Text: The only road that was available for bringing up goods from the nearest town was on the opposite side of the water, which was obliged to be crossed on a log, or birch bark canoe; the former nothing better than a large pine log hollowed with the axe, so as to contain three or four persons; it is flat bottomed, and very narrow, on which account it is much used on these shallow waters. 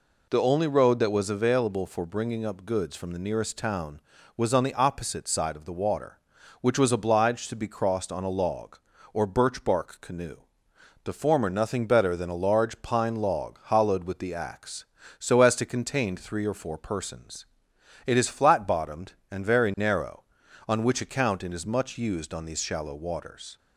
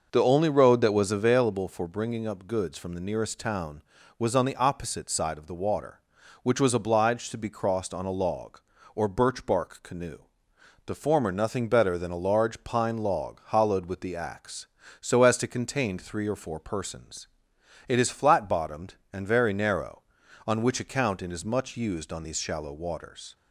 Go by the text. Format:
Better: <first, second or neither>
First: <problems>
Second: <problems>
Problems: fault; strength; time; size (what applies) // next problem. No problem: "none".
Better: first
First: none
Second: starts louder than the rest; noticeable; until 1.6 s; 5.5 dB